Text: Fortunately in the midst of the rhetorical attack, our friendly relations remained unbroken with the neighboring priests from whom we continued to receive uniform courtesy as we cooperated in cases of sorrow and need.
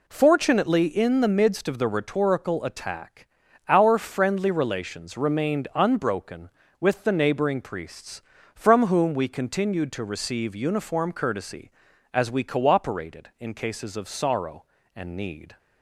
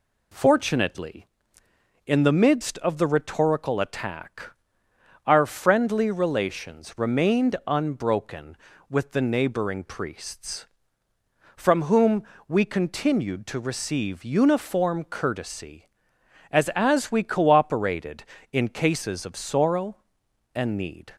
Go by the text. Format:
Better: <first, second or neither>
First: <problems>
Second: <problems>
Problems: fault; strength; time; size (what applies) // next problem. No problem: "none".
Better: first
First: none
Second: pauses between "whom" and "we"; slight; at 12.2 s; 0.24 s long // says "as" twice; at 16.7 s